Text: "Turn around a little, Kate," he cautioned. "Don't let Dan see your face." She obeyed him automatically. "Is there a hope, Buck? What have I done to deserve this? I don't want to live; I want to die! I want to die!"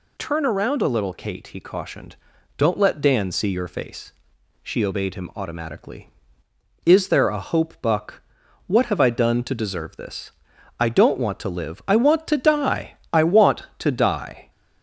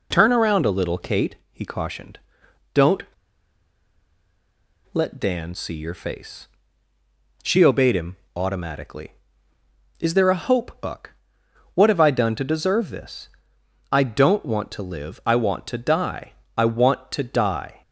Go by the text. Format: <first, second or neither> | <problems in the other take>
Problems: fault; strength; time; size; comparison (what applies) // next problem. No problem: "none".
first | pauses between "Don't" and "let"; strong; at 3.0 s; 1.8 s long // pauses between "him" and "automatically"; slight; at 8.1 s; 0.18 s long